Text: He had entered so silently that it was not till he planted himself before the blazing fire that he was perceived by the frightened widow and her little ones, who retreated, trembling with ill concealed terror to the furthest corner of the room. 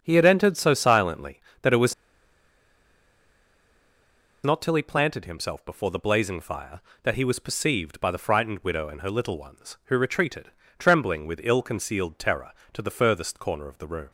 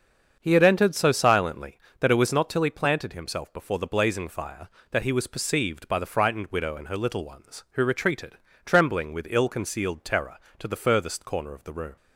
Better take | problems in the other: second | starts louder than the rest; until 1.0 s; 7 dB; also in the second // pauses between "was" and "not"; strong; at 1.9 s; 2.5 s long

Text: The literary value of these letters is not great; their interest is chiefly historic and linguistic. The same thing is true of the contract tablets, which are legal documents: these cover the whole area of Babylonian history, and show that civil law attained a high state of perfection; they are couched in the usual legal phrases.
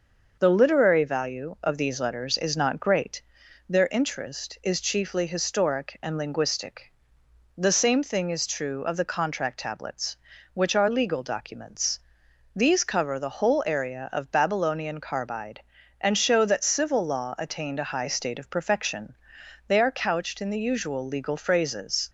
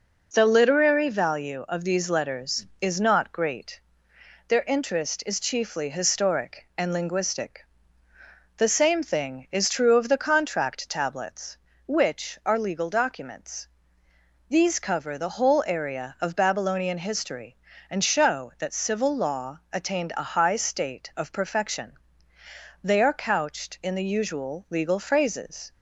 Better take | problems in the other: second | starts louder than the rest; noticeable; until 1.4 s; 6 dB // says "carbide" for "history"; at 15.0 s

